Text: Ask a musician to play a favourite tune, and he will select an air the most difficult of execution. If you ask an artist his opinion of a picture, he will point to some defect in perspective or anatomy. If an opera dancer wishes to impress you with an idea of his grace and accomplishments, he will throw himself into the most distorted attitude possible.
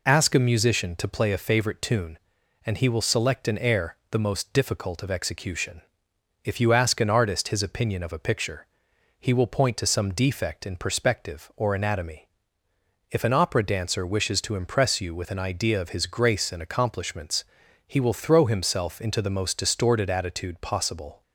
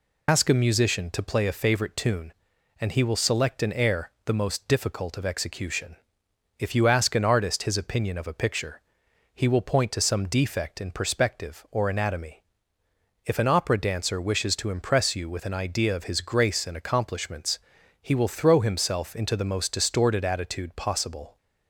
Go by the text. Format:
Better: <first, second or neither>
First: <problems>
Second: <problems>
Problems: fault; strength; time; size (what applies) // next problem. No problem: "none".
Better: first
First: none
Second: loses the start of "Ask"; at 0.2 s; 90 ms